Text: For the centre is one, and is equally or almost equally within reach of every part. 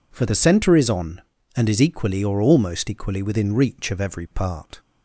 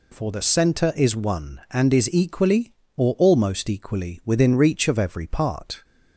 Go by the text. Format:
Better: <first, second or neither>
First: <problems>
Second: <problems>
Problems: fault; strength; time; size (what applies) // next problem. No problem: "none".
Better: second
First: says "on" for "one"; at 0.8 s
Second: none